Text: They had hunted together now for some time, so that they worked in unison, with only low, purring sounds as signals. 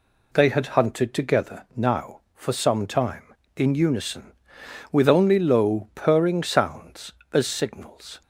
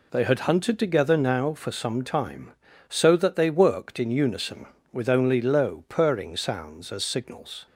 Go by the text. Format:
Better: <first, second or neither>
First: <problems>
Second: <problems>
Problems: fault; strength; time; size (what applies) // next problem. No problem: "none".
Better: second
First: skips "so that they worked"; at 3.4 s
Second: none